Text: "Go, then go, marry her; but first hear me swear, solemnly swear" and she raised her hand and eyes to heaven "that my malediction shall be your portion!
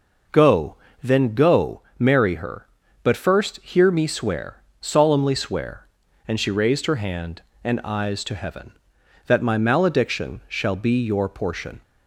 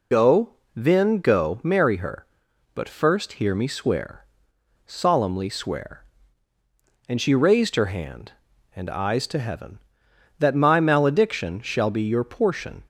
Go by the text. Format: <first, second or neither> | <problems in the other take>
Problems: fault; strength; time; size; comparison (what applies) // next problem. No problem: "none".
first | loses the start of "Go"; at 0.1 s; 30 ms